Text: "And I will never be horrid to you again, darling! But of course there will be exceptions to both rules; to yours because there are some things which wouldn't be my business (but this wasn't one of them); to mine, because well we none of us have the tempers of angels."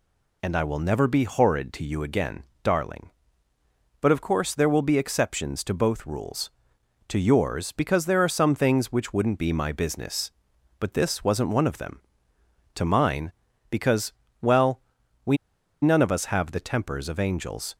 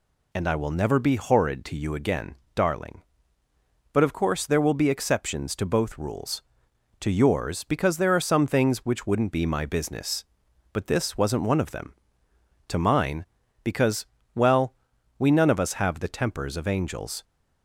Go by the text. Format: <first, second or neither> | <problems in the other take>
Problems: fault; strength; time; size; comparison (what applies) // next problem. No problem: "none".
second | pauses between "because" and "well"; slight; at 14.1 s; 0.30 s long; slight in the second // pauses between "well" and "we"; at 14.8 s; 0.42 s long; also in the second // pauses between "we" and "none"; noticeable; at 15.3 s; 0.46 s long